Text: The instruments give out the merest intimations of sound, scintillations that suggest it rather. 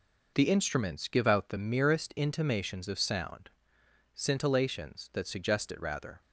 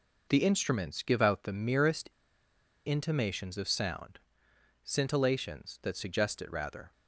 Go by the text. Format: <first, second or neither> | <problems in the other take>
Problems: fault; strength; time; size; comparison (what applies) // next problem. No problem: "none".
first | pauses between "merest" and "intimations"; noticeable; at 2.0 s; 0.76 s long